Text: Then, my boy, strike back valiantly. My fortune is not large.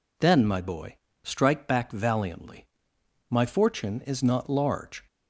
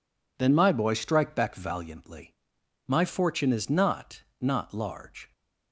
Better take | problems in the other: first | says "not" twice; at 4.3 s

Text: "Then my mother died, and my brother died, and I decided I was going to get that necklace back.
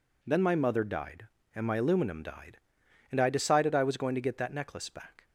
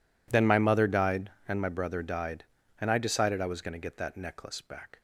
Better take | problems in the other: second | says "aluminum" for "brother"; at 1.7 s

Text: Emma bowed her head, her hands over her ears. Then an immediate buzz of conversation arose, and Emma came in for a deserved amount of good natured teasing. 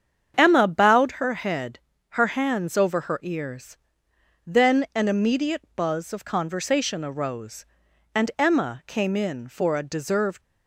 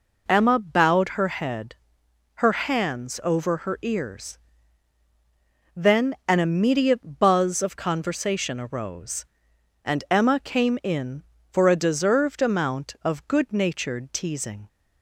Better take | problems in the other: second | starts louder than the rest; strong; until 1.3 s; 8 dB // stops before "amount of good natured teasing"; at 10.4 s

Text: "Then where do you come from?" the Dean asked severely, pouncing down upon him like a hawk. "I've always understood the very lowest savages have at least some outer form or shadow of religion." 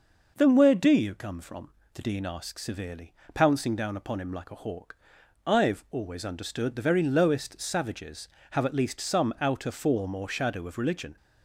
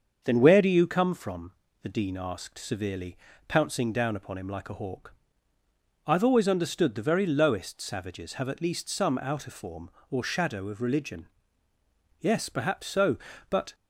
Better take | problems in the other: first | starts louder than the rest; until 1.2 s; 7 dB // goes on to say "Yes perhaps so but"; from 12.2 s on; 1.5 s long

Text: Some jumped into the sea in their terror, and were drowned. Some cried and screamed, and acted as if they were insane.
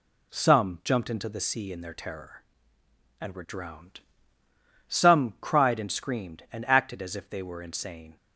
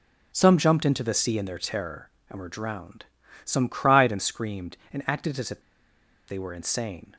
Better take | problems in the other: first | pauses between "if" and "they"; noticeable; at 5.6 s; 0.65 s long

